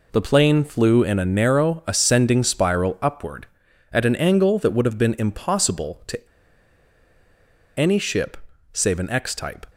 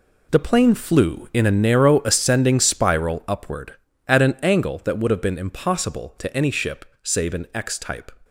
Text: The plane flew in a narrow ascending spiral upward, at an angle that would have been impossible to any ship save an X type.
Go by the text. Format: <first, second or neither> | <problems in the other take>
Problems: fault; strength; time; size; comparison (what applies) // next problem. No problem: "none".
second | pauses between "to" and "any"; strong; at 6.2 s; 1.5 s long // pauses between "ship" and "save"; slight; at 8.3 s; 0.36 s long; slight in the second